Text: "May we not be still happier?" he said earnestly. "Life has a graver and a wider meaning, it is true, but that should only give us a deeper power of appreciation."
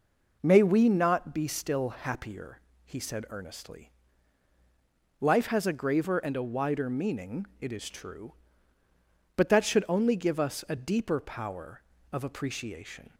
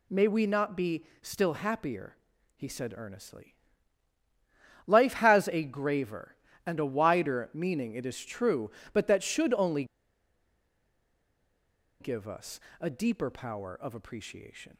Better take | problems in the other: first | pauses between "only" and "give"; strong; at 9.8 s; 2.1 s long // pauses between "us" and "a"; slight; at 12.5 s; 0.20 s long

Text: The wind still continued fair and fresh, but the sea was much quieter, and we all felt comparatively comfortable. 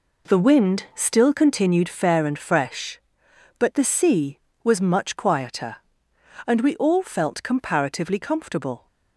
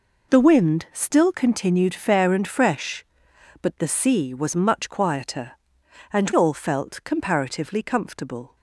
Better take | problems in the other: first | skips "we"; at 6.3 s

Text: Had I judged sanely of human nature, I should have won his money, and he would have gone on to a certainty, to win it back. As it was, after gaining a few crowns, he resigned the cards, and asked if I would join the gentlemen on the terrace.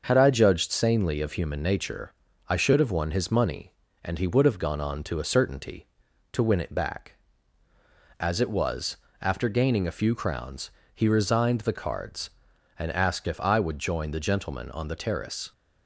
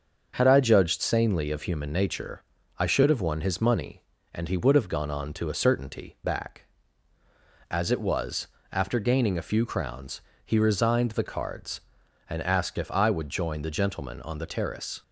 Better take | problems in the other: first | starts louder than the rest; until 1.3 s; 6.5 dB; also in the first // skips "to win it"; at 6.2 s

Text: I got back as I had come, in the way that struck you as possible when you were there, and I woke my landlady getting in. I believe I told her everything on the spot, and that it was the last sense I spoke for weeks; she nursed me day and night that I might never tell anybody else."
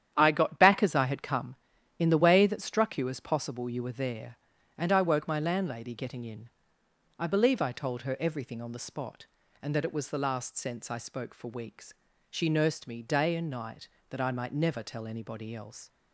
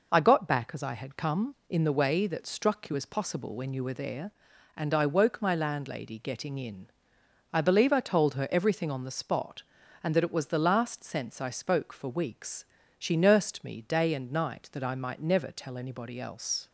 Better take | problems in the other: second | starts louder than the rest; strong; until 1.1 s; 10 dB // skips "when"; at 3.7 s

